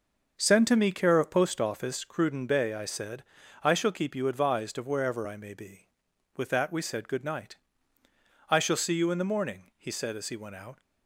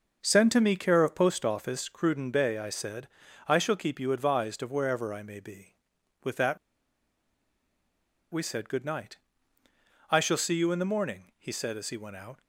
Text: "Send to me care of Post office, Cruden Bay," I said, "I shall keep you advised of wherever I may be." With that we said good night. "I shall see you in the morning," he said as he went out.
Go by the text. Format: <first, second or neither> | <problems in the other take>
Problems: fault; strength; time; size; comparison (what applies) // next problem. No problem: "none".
first | starts louder than the rest; until 1.2 s; 6 dB; noticeable in the first // pauses between "that" and "we"; strong; at 6.5 s; 1.7 s long